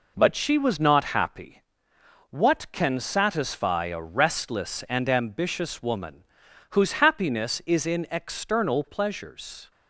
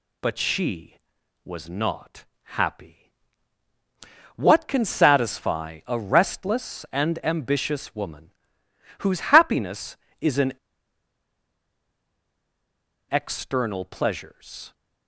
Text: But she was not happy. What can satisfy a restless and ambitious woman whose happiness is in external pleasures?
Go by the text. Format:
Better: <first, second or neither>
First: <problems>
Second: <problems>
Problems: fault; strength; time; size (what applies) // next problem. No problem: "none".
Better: first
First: pauses between "woman" and "whose"; noticeable; at 6.2 s; 0.46 s long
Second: pauses between "not" and "happy"; slight; at 2.2 s; 0.18 s long // pauses between "woman" and "whose"; noticeable; at 8.3 s; 0.68 s long // pauses between "in" and "external"; strong; at 10.5 s; 2.5 s long